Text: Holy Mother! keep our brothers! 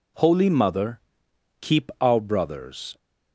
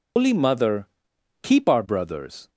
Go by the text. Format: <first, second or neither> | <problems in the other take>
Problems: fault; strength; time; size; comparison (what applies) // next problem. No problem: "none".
first | loses the start of "Holy"; at 0.1 s; 140 ms